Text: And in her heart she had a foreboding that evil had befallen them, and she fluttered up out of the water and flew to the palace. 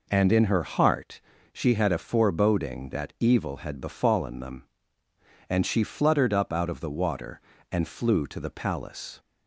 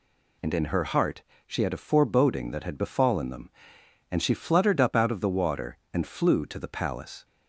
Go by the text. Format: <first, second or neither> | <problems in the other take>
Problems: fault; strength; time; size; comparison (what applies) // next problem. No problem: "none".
first | pauses between "heart" and "she"; slight; at 1.2 s; 0.24 s long; slight in the first // skips "evil"; at 2.6 s